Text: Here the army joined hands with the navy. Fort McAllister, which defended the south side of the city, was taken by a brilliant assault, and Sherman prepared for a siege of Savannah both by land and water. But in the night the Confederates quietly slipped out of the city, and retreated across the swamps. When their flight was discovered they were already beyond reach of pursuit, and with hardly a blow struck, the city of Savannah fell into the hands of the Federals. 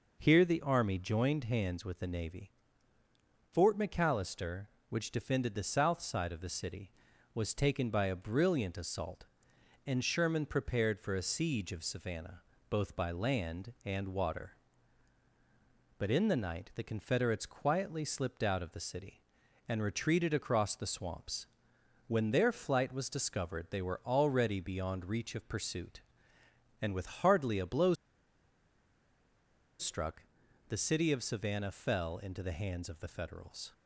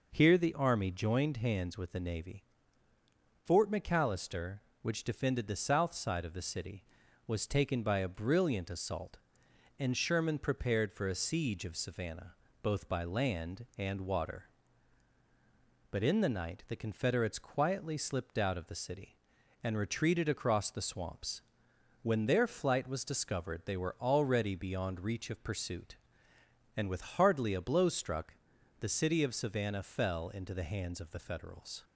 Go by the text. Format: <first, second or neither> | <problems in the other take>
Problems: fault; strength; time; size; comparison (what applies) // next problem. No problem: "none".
second | pauses between "Savannah" and "both"; slight; at 12.4 s; 0.28 s long; slight in the second // pauses between "blow" and "struck"; strong; at 27.9 s; 1.8 s long